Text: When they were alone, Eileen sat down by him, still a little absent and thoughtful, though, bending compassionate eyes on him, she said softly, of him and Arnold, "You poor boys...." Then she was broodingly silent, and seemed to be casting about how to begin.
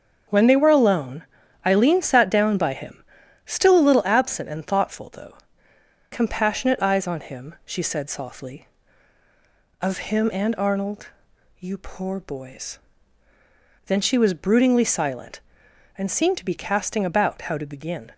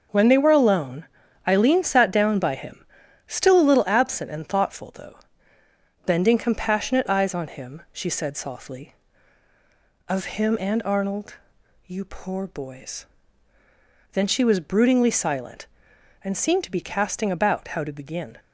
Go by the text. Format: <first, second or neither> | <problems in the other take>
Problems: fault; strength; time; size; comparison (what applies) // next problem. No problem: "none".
second | starts louder than the rest; strong; until 1.7 s; 7.5 dB; noticeable in the second // skips "bending"; at 5.7 s